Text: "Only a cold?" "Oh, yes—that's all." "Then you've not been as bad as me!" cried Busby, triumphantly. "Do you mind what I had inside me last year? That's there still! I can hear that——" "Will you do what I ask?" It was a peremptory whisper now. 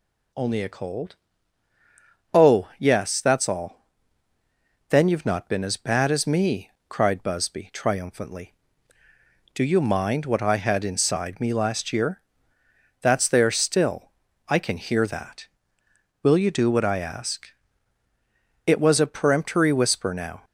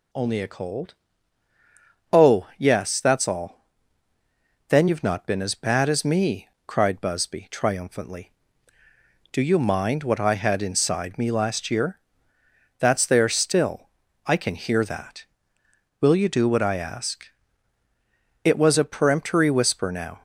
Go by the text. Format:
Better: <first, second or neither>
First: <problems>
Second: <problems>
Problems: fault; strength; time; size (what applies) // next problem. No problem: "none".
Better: neither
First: none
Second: none